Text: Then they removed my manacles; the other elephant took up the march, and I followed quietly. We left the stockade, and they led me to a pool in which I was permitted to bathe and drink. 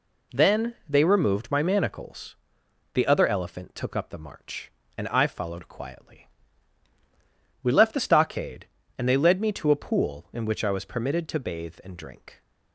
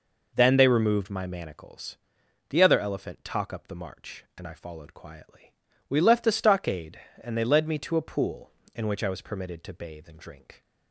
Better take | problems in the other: first | says "talk" for "took"; at 3.2 s

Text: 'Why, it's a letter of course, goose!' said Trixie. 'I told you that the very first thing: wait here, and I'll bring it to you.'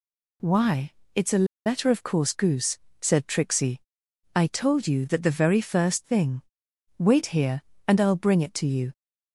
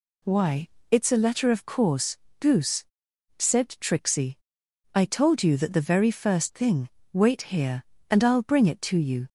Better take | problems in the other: second | pauses between "a" and "letter"; slight; at 1.4 s; 0.20 s long

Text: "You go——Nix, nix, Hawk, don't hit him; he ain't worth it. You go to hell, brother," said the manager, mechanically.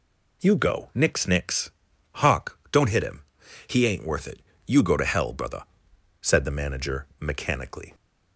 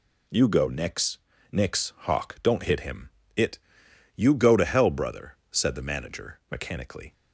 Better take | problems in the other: first | skips "he ain't worth"; at 3.2 s

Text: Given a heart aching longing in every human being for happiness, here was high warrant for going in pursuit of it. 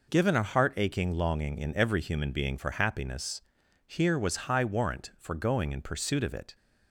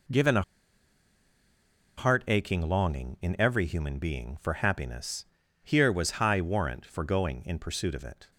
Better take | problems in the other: first | pauses between "a" and "heart"; strong; at 0.4 s; 1.5 s long

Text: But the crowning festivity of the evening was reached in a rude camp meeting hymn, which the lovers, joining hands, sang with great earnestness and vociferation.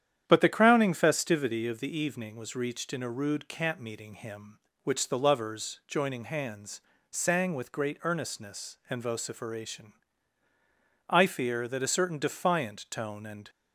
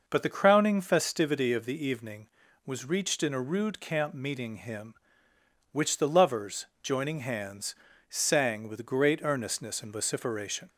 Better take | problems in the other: second | starts louder than the rest; strong; until 1.2 s; 9.5 dB // goes on to say "I fear that a certain defiant tone and"; strong; from 11.0 s on; 2.4 s long

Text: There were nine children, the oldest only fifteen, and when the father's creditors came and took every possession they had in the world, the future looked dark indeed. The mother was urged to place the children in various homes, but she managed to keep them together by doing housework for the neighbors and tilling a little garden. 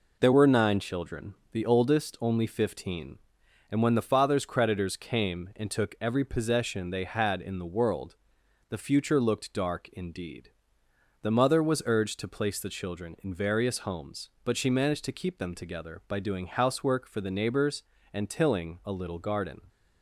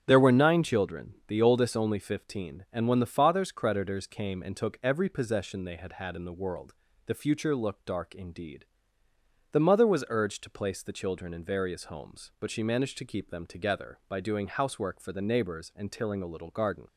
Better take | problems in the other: first | starts louder than the rest; strong; until 1.0 s; 10 dB // says "had" twice; at 5.9 s

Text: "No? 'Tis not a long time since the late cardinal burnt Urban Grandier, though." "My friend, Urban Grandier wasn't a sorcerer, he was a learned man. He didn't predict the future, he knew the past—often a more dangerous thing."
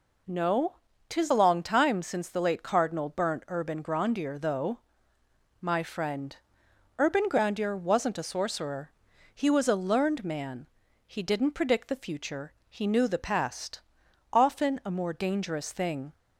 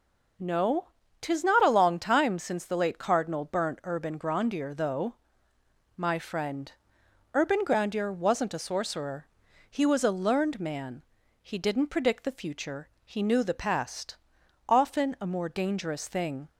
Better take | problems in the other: second | skips "not"; at 1.3 s

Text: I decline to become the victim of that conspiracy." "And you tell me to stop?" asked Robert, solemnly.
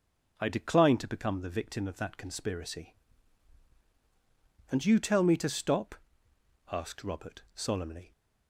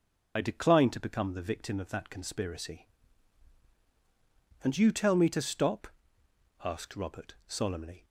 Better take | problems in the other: first | loses the start of "I"; at 0.3 s; 55 ms

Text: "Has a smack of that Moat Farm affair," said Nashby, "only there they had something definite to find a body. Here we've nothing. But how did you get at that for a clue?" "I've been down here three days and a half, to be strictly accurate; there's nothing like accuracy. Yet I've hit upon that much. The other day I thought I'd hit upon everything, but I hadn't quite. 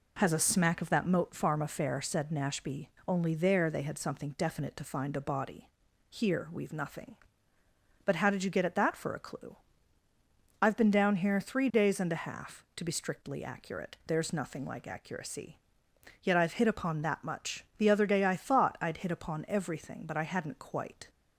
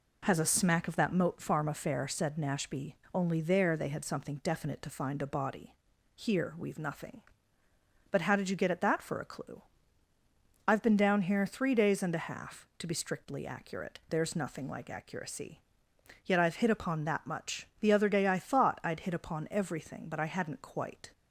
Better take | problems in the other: neither | none

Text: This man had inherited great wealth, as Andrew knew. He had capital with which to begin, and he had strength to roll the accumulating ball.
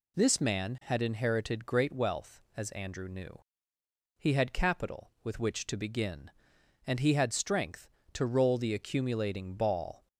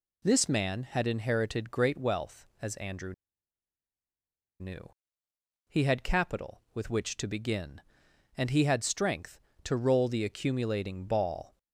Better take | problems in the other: first | pauses between "Andrew" and "knew"; strong; at 3.1 s; 1.4 s long

